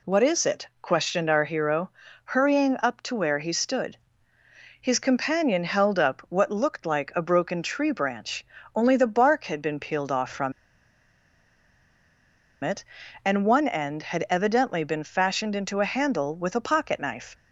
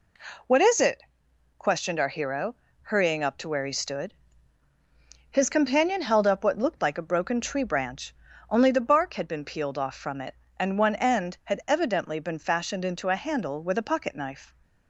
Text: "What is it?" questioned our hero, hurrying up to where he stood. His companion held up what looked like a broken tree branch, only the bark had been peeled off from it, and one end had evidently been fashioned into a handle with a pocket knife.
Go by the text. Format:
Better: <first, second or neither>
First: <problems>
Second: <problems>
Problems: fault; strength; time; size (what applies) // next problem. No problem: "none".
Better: second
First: pauses between "from" and "it"; strong; at 10.5 s; 2.1 s long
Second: none